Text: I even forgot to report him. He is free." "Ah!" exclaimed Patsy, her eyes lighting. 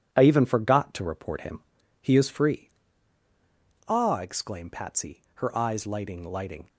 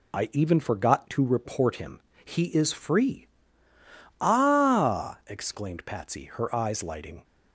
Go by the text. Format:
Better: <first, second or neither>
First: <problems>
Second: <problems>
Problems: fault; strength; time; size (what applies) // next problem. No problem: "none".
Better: second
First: says "lighting" twice; at 6.2 s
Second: none